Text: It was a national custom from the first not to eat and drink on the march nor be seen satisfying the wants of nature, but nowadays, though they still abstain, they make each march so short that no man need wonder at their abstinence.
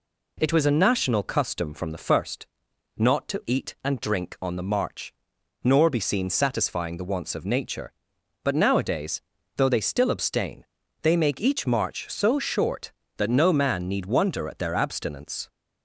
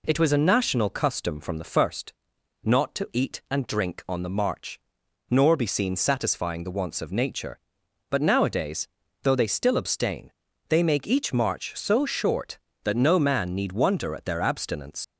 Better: first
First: pauses between "first" and "not"; noticeable; at 2.4 s; 0.50 s long // pauses between "march" and "nor"; noticeable; at 5.1 s; 0.52 s long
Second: pauses between "first" and "not"; noticeable; at 2.1 s; 0.50 s long // pauses between "march" and "nor"; noticeable; at 4.7 s; 0.52 s long // leaves "abstinence" unfinished; at 15.0 s; 105 ms

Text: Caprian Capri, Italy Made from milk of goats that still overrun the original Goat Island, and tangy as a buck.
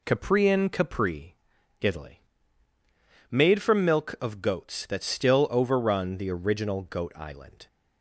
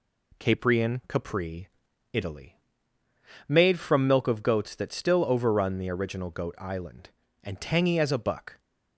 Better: second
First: pauses between "Italy" and "Made"; at 2.1 s; 1.1 s long // stops before "and tangy as a buck"; at 7.6 s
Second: pauses between "Italy" and "Made"; noticeable; at 2.5 s; 0.90 s long

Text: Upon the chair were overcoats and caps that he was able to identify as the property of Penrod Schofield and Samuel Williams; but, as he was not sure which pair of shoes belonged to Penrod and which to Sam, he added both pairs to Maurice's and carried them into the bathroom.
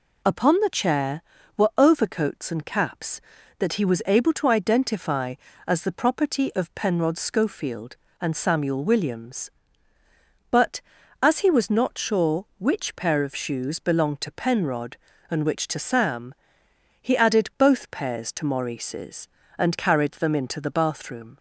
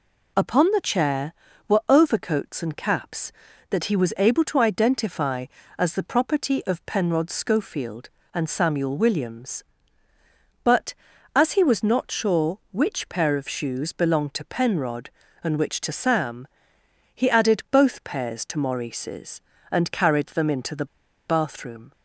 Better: first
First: none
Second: pauses between "the" and "bathroom"; at 20.8 s; 0.41 s long

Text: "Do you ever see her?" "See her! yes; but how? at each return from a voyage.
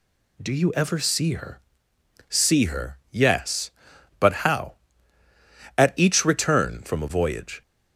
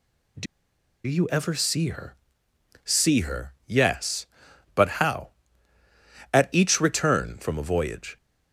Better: first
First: none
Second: pauses between "Do" and "you"; noticeable; at 0.4 s; 0.60 s long

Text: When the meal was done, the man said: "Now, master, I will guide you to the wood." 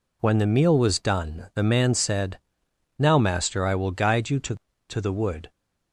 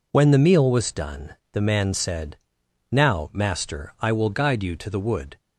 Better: second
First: says "to" twice; at 4.8 s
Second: none

